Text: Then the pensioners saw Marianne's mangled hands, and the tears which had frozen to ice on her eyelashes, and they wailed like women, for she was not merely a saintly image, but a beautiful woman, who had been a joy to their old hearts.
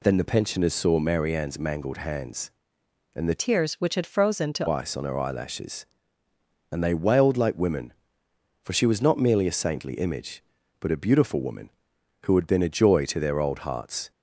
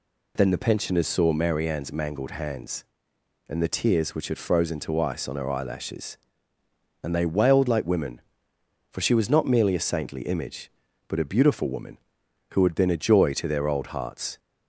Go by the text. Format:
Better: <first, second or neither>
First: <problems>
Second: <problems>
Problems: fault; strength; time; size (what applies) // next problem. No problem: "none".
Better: second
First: changes voice from "tears" to "to"; from 3.3 to 4.6 s; 1.3 s long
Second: none